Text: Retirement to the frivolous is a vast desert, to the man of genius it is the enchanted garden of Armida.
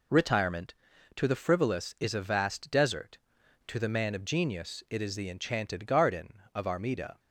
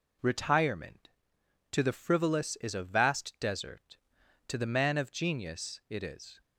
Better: first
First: none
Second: stops before "the enchanted garden of Armida"; at 6.4 s

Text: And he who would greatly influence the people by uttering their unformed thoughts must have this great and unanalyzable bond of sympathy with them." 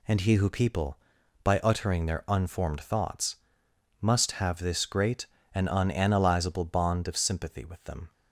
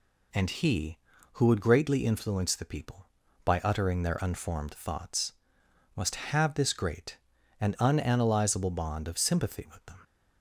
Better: second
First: skips "would greatly influence the"; at 0.4 s // pauses between "thoughts" and "must"; noticeable; at 3.3 s; 0.64 s long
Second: pauses between "thoughts" and "must"; noticeable; at 5.3 s; 0.62 s long

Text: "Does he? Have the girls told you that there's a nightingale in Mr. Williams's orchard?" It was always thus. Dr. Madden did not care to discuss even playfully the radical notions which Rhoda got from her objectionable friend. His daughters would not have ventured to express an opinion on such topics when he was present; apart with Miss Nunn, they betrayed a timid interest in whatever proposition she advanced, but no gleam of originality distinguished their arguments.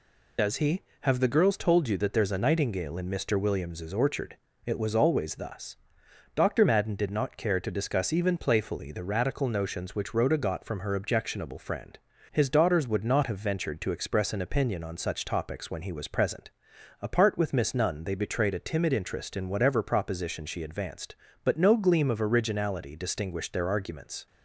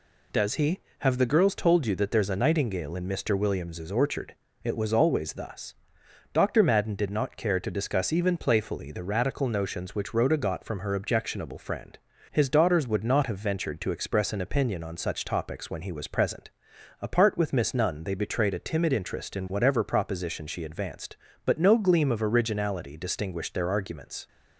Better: second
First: loses the start of "Does"; at 0.3 s; 50 ms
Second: none

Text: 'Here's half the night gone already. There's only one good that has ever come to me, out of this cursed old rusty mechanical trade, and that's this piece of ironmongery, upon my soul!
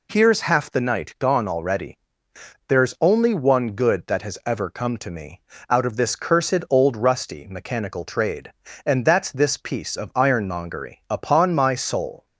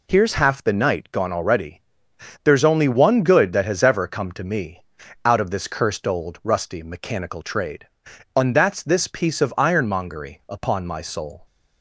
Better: neither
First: none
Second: none

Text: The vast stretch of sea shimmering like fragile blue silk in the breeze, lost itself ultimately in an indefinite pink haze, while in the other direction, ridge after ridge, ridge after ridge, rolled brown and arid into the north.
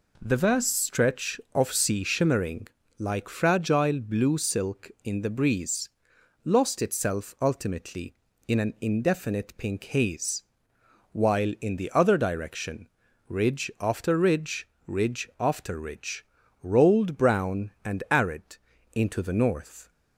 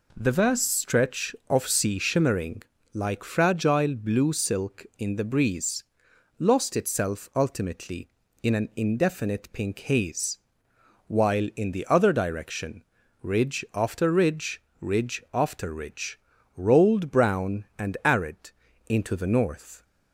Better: neither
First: pauses between "shimmering" and "like"; slight; at 2.6 s; 0.30 s long // pauses between "arid" and "into"; at 18.5 s; 0.38 s long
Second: pauses between "shimmering" and "like"; slight; at 2.6 s; 0.30 s long // pauses between "arid" and "into"; at 18.4 s; 0.38 s long

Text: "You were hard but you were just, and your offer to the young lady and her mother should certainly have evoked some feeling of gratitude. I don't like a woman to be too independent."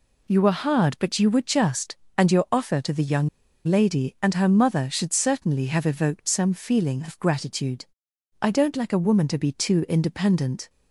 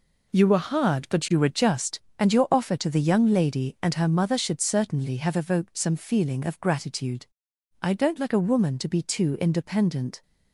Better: second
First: pauses between "young" and "lady"; at 3.2 s; 0.38 s long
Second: none

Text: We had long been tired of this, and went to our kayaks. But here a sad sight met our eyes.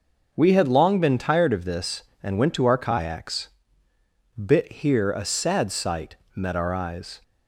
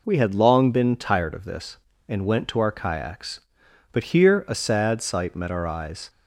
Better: second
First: says "Bit" for "But"; at 4.3 s // pauses between "sight" and "met"; slight; at 6.1 s; 0.20 s long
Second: none

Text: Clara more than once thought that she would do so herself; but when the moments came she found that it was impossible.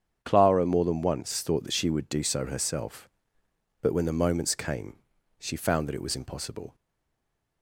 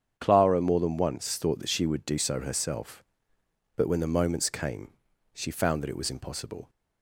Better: second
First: starts louder than the rest; strong; until 1.2 s; 8 dB // pauses between "came" and "she"; at 4.9 s; 0.42 s long // stays silent after the last word; slight; from 6.7 s on; 0.9 s long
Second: starts louder than the rest; strong; until 1.1 s; 8 dB // pauses between "came" and "she"; at 4.9 s; 0.42 s long

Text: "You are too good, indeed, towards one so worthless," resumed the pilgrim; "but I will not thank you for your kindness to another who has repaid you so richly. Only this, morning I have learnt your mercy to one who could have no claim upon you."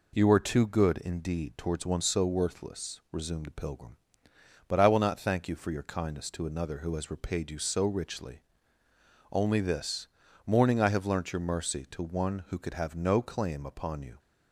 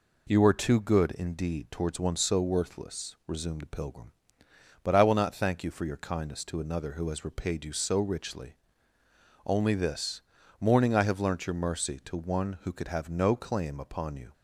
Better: neither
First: none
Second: none

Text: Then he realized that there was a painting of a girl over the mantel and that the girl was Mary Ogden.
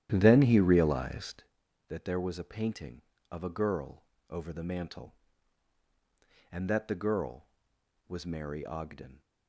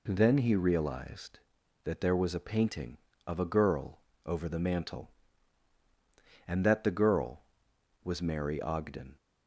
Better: second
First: starts louder than the rest; strong; until 1.5 s; 11.5 dB // pauses between "girl" and "over"; slight; at 4.0 s; 0.26 s long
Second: pauses between "girl" and "over"; slight; at 3.9 s; 0.26 s long

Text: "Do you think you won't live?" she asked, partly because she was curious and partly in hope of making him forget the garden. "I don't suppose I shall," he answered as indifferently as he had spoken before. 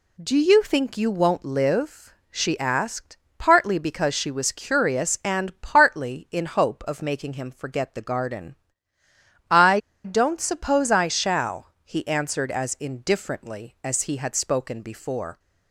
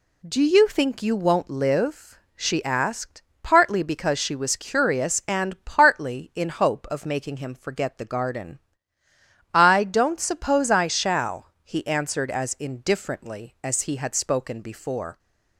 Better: second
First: pauses between "I" and "don't"; slight; at 9.7 s; 0.25 s long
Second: none

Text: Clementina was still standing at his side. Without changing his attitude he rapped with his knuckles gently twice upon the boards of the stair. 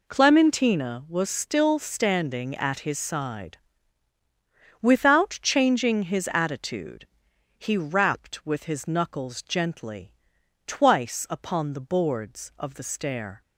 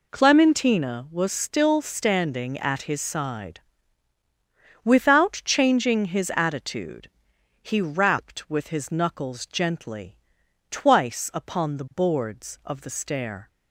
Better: neither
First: pauses between "attitude" and "he"; noticeable; at 7.0 s; 0.48 s long // pauses between "gently" and "twice"; noticeable; at 10.1 s; 0.54 s long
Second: pauses between "attitude" and "he"; noticeable; at 7.1 s; 0.50 s long // pauses between "gently" and "twice"; noticeable; at 10.1 s; 0.54 s long

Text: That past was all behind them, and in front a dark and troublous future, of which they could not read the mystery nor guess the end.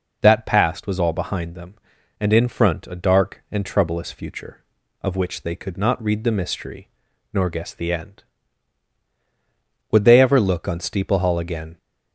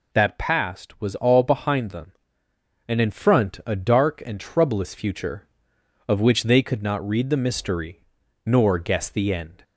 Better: second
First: pauses between "mystery" and "nor"; at 6.8 s; 0.44 s long // goes on to say "Would they ever look on Steeple Hall again"; strong; from 9.9 s on; 1.8 s long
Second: pauses between "mystery" and "nor"; at 8.0 s; 0.42 s long

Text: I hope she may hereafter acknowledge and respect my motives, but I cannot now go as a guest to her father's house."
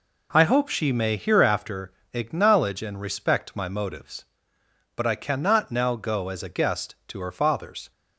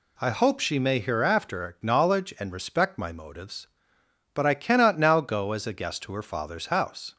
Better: second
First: pauses between "hereafter" and "acknowledge"; slight; at 1.9 s; 0.22 s long // stops before "house"; at 7.9 s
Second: none

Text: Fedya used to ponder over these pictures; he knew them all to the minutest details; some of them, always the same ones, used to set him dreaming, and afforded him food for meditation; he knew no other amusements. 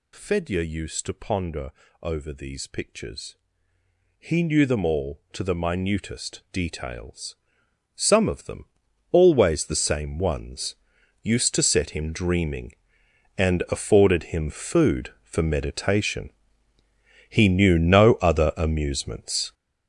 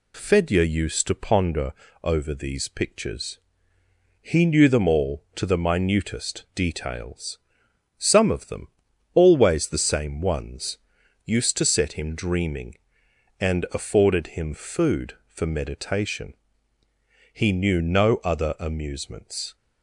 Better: second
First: gets louder; strong; throughout; 9.5 dB // pauses between "ponder" and "over"; slight; at 1.7 s; 0.28 s long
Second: pauses between "ponder" and "over"; slight; at 1.7 s; 0.28 s long

